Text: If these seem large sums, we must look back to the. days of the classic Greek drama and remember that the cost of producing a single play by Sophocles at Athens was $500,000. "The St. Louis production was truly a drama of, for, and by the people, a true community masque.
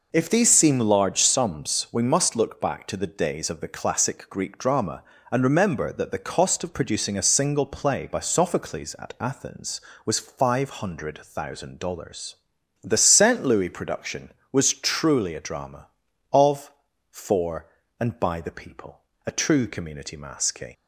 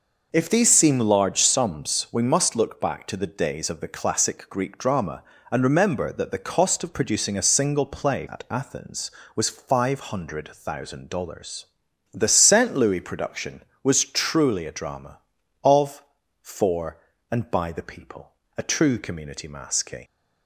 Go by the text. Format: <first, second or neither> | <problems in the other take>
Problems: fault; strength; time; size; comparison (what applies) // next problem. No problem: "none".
first | skips "by Sophocles"; at 8.2 s